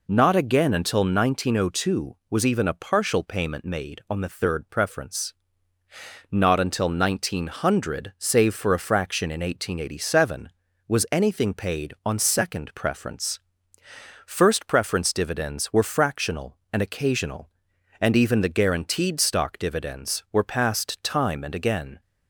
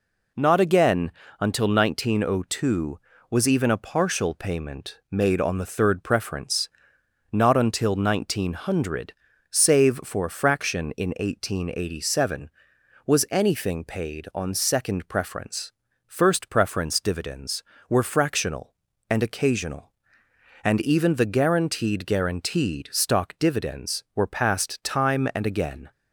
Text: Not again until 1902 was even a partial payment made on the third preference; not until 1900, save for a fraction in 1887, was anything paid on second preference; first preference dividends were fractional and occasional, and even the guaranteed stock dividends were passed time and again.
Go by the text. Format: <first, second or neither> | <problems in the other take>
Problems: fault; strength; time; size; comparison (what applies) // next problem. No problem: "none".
first | pauses between "again" and "until"; slight; at 1.1 s; 0.28 s long // says "guaranteed" twice; at 22.0 s